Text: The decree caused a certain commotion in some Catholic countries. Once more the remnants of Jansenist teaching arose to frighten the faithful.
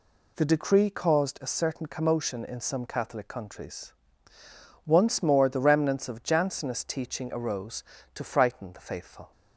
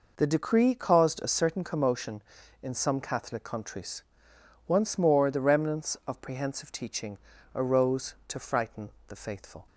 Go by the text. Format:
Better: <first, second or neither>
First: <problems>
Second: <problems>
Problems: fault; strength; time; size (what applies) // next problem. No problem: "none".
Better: first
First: none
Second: says "Prehensive" for "Jansenist"; at 6.2 s // pauses between "teaching" and "arose"; at 7.1 s; 0.38 s long // pauses between "frighten" and "the"; slight; at 8.9 s; 0.18 s long